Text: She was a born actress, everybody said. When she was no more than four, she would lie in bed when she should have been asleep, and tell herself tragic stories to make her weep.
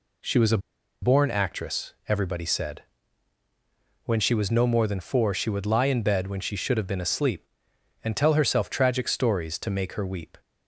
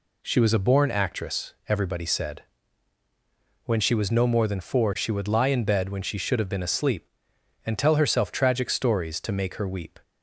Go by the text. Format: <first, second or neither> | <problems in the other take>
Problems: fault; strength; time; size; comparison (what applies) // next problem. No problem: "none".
second | pauses between "a" and "born"; at 0.5 s; 0.44 s long